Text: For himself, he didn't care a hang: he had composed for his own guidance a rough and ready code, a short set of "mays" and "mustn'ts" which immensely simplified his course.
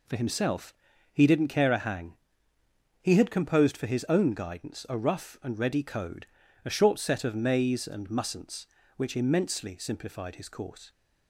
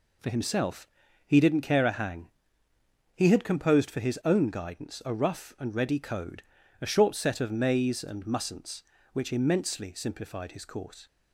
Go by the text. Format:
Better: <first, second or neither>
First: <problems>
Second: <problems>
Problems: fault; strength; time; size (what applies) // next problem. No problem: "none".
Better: neither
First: none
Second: none